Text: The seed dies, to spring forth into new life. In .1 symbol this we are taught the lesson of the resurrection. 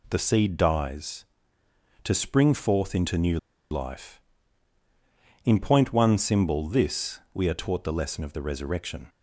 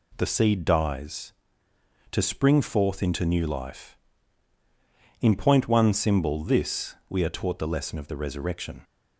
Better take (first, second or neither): second